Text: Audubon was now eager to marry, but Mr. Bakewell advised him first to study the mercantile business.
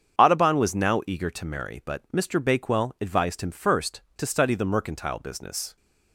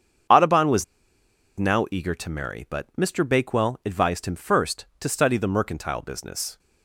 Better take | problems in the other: first | starts louder than the rest; strong; until 2.0 s; 7.5 dB; strong in the first // pauses between "was" and "now"; noticeable; at 0.8 s; 0.73 s long

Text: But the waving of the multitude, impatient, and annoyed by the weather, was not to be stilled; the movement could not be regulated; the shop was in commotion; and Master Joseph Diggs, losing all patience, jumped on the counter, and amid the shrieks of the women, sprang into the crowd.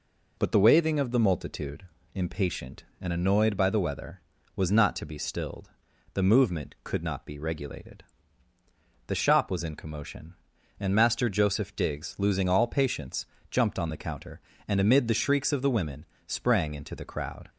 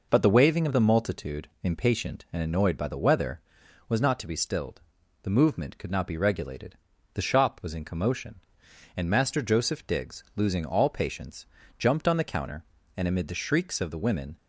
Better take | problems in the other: first | stops before "sprang into the crowd"; at 14.3 s

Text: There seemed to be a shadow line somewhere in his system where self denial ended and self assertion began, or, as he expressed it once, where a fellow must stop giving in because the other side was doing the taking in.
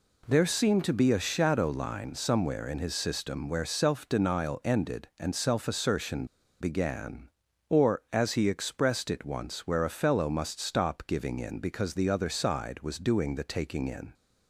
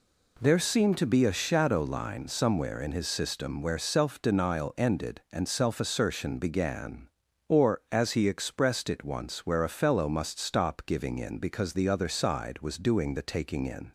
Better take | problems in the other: second | pauses between "assertion" and "began"; slight; at 6.2 s; 0.36 s long

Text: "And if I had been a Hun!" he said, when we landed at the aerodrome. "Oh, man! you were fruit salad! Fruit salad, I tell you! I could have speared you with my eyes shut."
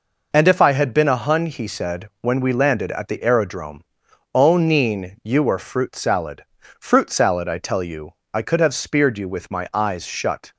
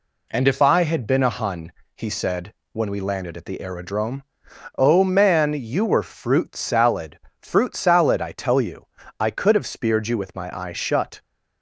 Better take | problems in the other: second | says "neen" for "man"; at 4.5 s

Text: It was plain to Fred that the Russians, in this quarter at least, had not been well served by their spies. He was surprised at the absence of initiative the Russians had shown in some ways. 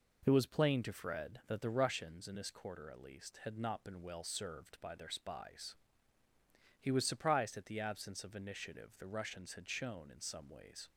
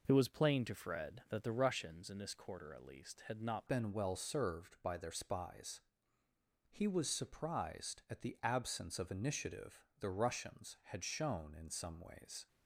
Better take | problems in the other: first | changes voice at "been"; from 3.6 s on; 8.8 s long // pauses between "initiative" and "the"; slight; at 9.8 s; 0.16 s long

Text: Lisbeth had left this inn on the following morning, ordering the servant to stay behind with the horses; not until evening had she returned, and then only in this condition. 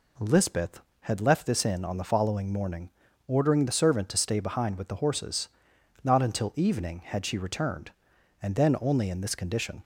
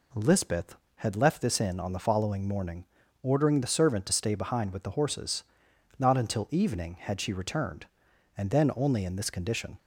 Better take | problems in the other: neither | none

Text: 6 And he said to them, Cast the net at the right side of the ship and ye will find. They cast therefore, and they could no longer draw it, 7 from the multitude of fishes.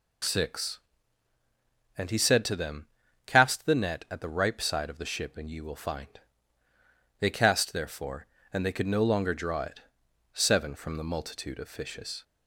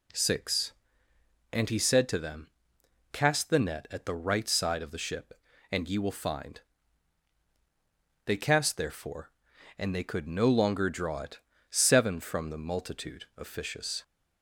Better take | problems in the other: second | says "ripe" for "right"; at 4.2 s

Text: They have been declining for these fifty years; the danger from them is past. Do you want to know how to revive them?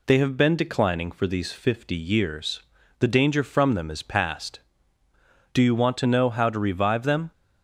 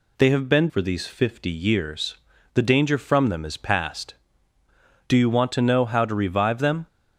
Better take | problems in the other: first | skips "declining"; at 0.6 s

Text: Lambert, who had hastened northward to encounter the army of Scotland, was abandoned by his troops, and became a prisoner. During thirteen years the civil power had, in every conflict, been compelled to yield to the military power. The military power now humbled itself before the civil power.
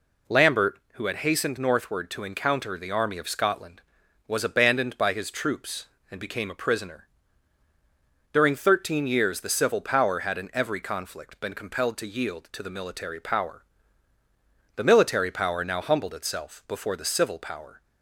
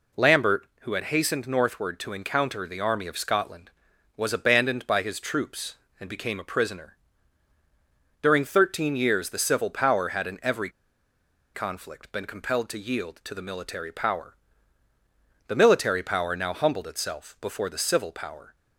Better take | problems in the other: first | pauses between "every" and "conflict"; noticeable; at 10.6 s; 0.85 s long

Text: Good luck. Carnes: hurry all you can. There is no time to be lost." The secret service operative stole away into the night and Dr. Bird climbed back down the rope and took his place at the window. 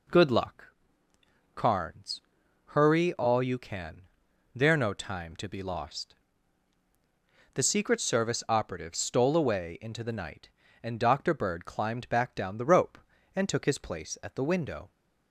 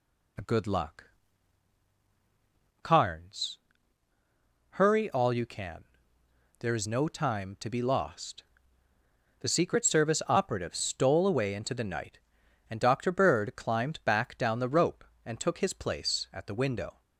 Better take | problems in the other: second | skips "is"; at 4.7 s

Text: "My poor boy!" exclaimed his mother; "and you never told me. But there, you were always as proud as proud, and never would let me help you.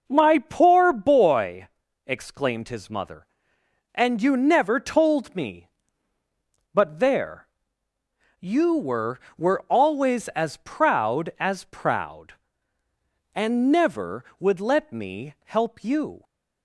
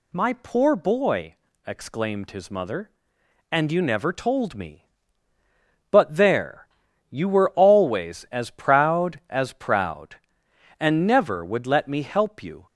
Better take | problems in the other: second | says "were" twice; at 9.3 s

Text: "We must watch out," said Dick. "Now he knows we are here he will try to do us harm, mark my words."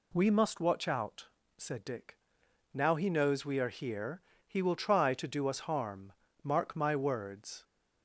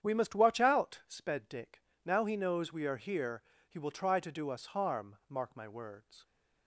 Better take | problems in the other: first | starts louder than the rest; strong; until 1.0 s; 9 dB // says "sped" for "said"; at 1.0 s // pauses between "here" and "he"; slight; at 3.4 s; 0.26 s long; slight in the first

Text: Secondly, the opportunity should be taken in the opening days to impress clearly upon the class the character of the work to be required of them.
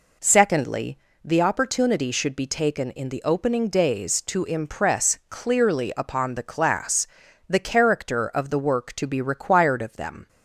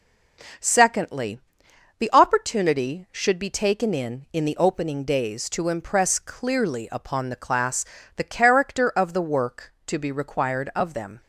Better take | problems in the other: first | says "in" twice; at 4.3 s // pauses between "class" and "the"; slight; at 7.8 s; 0.32 s long; also in the first

